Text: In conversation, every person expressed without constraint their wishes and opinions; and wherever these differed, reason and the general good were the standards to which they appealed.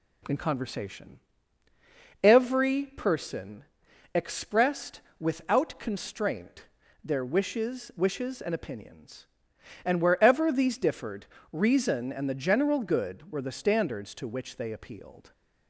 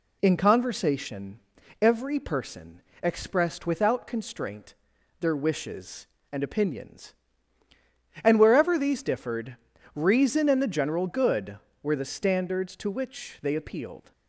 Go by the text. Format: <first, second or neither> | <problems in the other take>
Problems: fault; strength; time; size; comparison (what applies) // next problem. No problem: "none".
second | pauses between "person" and "expressed"; noticeable; at 3.6 s; 0.50 s long; slight in the second // pauses between "expressed" and "without"; slight; at 5.0 s; 0.18 s long // pauses between "constraint" and "their"; at 6.6 s; 0.38 s long; noticeable in the second // says "wishes" twice; at 7.9 s